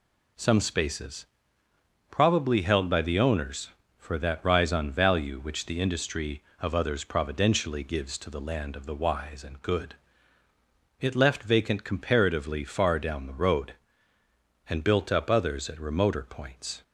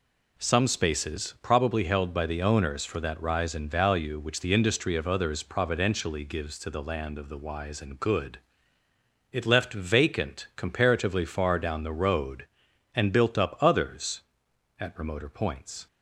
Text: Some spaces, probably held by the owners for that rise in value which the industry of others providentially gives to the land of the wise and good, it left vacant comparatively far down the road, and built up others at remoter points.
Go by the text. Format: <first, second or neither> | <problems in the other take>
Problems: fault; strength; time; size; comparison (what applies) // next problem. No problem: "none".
second | says "on" for "in"; at 4.7 s